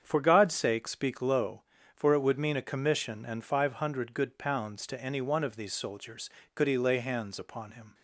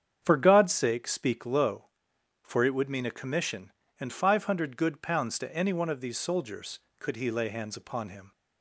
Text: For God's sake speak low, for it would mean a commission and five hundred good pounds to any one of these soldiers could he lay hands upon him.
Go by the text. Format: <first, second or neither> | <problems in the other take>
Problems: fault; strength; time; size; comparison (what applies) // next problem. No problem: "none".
neither | starts louder than the rest; strong; the same in both